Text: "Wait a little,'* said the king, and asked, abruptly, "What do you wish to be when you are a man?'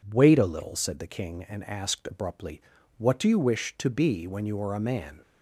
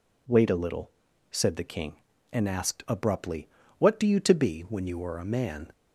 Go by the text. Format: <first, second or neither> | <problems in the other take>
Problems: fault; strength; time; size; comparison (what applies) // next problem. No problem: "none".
first | skips "wish"; at 4.1 s